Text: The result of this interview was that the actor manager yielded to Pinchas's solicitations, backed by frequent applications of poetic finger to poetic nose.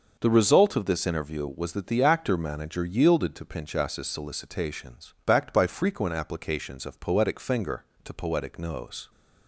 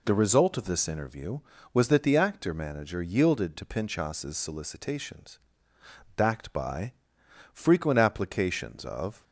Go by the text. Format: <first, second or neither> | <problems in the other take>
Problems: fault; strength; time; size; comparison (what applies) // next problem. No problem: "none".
first | pauses between "by" and "frequent"; noticeable; at 6.9 s; 0.60 s long // stops before "poetic finger to poetic nose"; at 9.2 s